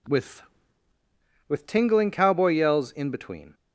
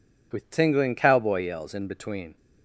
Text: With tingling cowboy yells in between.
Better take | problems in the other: second | says "With" twice; at 1.4 s

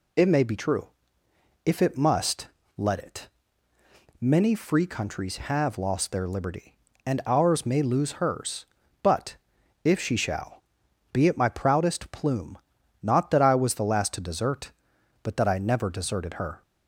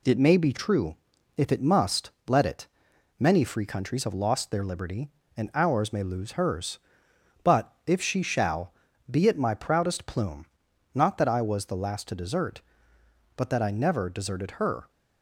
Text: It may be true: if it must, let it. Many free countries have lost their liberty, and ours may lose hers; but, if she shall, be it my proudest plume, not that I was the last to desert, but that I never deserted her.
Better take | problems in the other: neither | none

